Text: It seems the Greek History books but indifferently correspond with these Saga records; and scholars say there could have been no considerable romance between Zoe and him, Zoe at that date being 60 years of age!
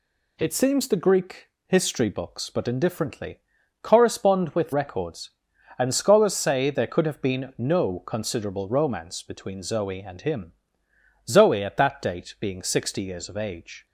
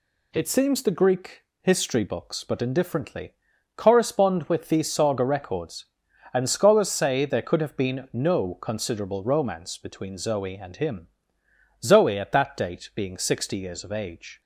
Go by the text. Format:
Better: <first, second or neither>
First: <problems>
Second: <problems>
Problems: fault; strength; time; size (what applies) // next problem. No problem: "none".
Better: second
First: pauses between "Greek" and "History"; slight; at 1.4 s; 0.20 s long // pauses between "indifferently" and "correspond"; at 3.3 s; 0.44 s long // skips "these Saga"; at 4.7 s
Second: pauses between "Greek" and "History"; slight; at 1.4 s; 0.20 s long // pauses between "indifferently" and "correspond"; at 3.3 s; 0.44 s long